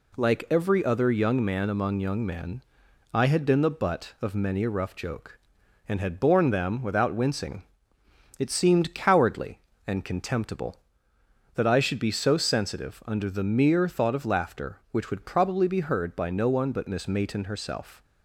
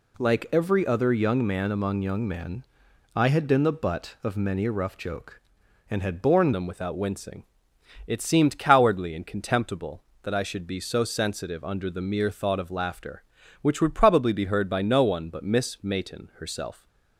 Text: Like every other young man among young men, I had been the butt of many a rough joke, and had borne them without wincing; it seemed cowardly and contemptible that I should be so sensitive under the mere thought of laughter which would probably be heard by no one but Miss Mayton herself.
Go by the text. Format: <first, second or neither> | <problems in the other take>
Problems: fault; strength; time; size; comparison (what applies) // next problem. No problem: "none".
first | changes voice at "them"; from 6.5 s on; 10.3 s long